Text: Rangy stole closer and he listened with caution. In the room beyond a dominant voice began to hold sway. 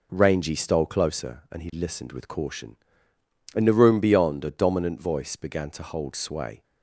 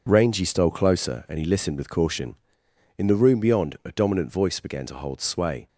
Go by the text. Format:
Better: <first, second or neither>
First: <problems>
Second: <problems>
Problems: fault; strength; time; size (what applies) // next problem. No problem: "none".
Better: neither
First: none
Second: none